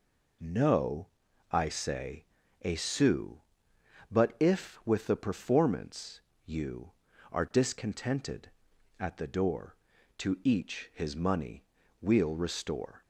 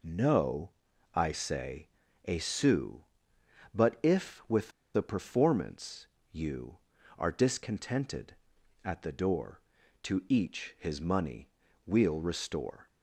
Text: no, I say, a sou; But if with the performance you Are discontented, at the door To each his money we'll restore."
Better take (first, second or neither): first